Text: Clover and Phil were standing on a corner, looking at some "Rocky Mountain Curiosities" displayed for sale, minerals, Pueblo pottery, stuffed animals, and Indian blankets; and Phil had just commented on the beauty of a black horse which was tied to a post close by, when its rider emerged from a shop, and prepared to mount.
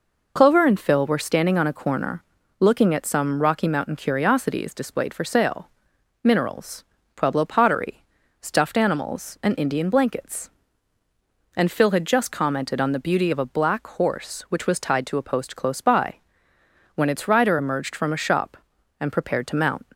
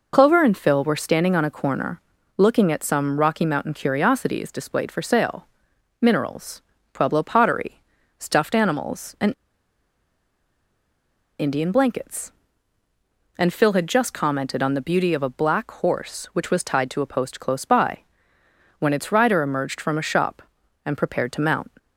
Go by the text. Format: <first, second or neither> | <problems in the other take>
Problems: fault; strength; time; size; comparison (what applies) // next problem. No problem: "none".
first | pauses between "and" and "Indian"; strong; at 9.3 s; 2.0 s long